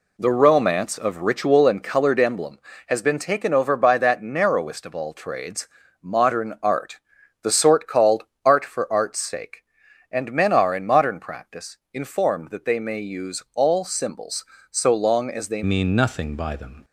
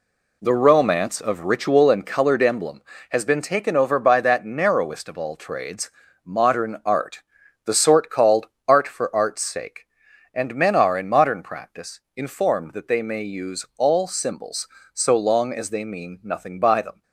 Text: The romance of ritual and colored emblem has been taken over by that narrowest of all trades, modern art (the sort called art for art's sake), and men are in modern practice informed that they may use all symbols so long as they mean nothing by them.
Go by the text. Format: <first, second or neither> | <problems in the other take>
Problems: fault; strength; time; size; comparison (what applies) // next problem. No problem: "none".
second | pauses between "called" and "art"; slight; at 8.2 s; 0.20 s long; slight in the second // pauses between "practice" and "informed"; slight; at 11.7 s; 0.16 s long; slight in the second // changes voice at "mean"; from 15.6 s on; 1.2 s long